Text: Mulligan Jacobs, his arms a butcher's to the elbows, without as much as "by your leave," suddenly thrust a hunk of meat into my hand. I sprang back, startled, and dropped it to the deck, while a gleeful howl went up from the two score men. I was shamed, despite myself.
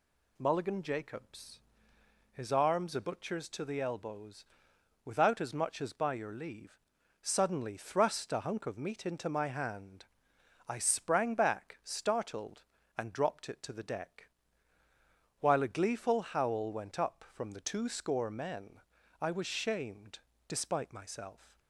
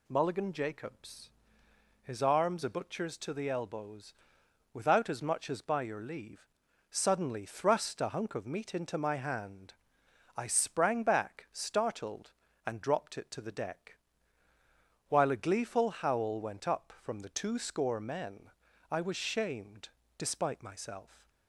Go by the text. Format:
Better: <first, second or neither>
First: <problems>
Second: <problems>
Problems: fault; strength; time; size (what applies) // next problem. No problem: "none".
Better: neither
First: none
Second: none